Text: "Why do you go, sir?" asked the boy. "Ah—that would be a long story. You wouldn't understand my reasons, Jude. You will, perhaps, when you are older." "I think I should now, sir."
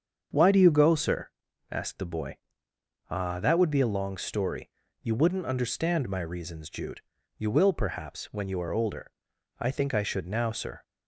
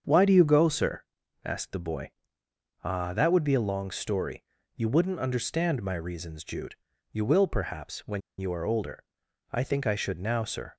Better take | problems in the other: first | starts louder than the rest; strong; until 1.4 s; 7 dB; strong in the first // pauses between "when" and "you"; slight; at 8.2 s; 0.18 s long

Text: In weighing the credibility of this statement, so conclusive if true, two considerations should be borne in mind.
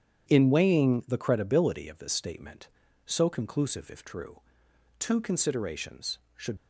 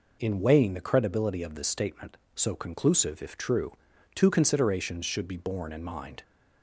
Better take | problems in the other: second | starts louder than the rest; strong; until 1.3 s; 9 dB // stops before "be borne in mind"; at 6.5 s

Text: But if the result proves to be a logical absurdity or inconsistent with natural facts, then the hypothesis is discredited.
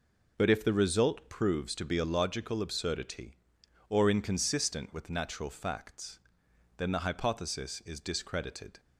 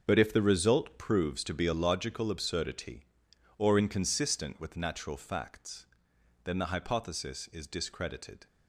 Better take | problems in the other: first | gets quieter; strong; throughout; 11 dB

